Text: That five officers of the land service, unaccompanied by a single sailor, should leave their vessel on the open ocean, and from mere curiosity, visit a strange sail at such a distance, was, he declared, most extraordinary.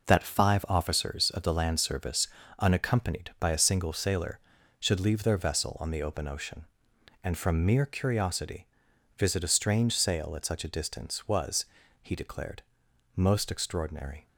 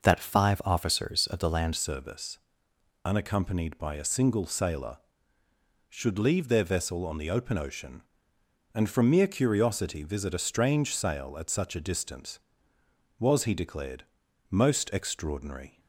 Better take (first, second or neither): first